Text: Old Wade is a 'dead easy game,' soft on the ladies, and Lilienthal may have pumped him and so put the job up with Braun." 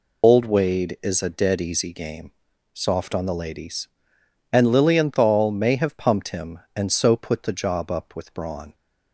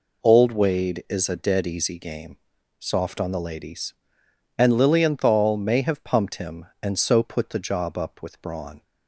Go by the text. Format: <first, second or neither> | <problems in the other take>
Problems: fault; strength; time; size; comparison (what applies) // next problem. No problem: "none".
second | loses the start of "Old"; at 0.2 s; 75 ms